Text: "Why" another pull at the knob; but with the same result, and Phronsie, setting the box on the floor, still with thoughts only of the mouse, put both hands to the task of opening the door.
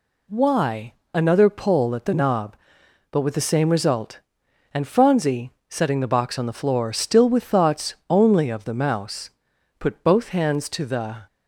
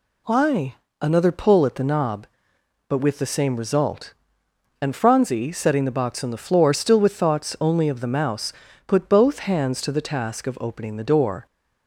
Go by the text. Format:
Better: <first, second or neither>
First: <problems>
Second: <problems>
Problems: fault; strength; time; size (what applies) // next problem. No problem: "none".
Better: second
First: pauses between "Why" and "another"; slight; at 0.9 s; 0.22 s long // pauses between "thoughts" and "only"; slight; at 7.9 s; 0.16 s long // stops before "task of opening the door"; at 11.2 s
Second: pauses between "Why" and "another"; slight; at 0.7 s; 0.30 s long